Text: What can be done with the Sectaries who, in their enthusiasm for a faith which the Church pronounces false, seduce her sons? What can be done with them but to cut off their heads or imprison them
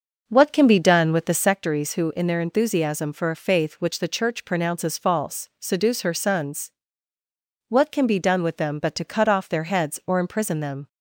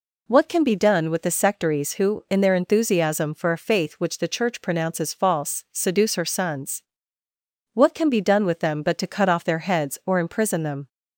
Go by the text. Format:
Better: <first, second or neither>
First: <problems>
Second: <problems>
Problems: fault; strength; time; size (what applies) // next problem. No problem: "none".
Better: second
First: starts louder than the rest; noticeable; until 1.6 s; 6 dB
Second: none